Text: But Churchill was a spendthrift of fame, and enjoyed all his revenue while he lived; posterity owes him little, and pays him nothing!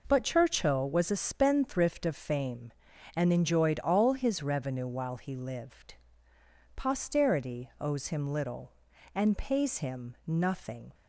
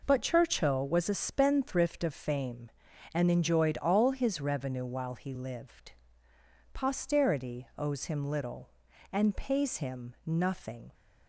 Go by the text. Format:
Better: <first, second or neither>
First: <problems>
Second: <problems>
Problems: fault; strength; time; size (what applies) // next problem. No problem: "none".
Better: neither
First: none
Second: none